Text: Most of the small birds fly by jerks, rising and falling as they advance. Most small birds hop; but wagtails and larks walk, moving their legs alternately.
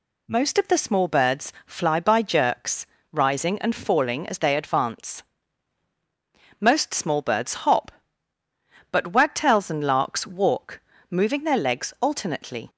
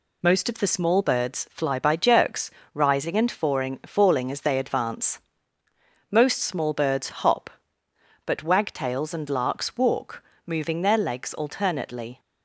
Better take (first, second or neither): first